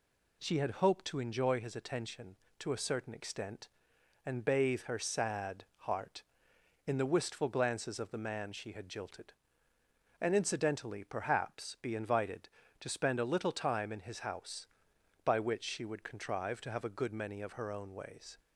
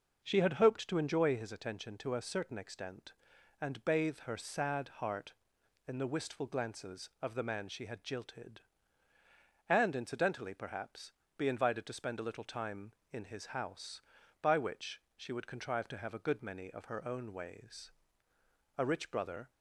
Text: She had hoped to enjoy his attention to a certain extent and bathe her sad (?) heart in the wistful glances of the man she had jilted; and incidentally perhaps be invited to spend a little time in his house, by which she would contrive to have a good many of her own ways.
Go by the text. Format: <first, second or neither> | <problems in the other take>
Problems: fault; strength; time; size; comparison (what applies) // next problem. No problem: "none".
first | pauses between "perhaps" and "be"; slight; at 11.1 s; 0.24 s long // pauses between "which" and "she"; slight; at 15.0 s; 0.16 s long // goes on to say "A rich brother"; noticeable; from 18.7 s on; 0.72 s long